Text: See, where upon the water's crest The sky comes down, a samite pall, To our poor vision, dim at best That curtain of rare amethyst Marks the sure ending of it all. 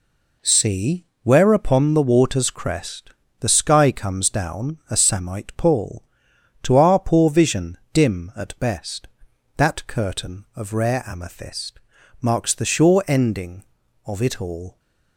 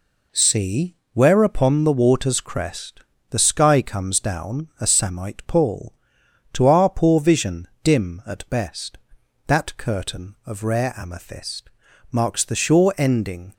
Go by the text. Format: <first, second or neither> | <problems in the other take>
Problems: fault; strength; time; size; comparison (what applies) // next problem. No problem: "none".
first | pauses between "crest" and "The"; slight; at 3.0 s; 0.30 s long; slight in the first // pauses between "amethyst" and "Marks"; at 11.6 s; 0.42 s long; also in the first // stops before "of it all"; at 13.5 s